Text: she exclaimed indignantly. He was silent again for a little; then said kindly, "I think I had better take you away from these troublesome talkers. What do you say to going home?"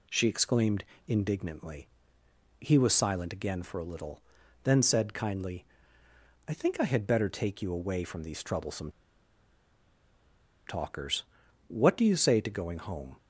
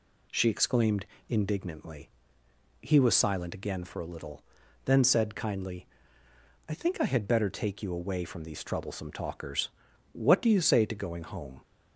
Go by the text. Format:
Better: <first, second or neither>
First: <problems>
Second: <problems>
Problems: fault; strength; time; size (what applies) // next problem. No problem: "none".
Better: second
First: pauses between "exclaimed" and "indignantly"; slight; at 0.8 s; 0.22 s long // pauses between "troublesome" and "talkers"; strong; at 8.8 s; 1.7 s long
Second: pauses between "exclaimed" and "indignantly"; slight; at 1.0 s; 0.22 s long